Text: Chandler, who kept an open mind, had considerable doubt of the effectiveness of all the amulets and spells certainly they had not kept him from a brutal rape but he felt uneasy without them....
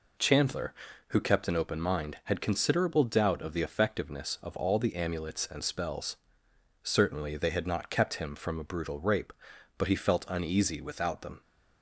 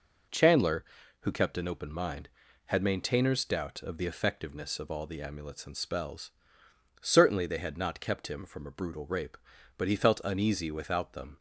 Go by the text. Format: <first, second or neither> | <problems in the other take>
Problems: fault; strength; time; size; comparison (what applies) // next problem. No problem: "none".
first | says "maintainers" for "considerable"; at 2.8 s // pauses between "spells" and "certainly"; noticeable; at 6.3 s; 0.70 s long; noticeable in the first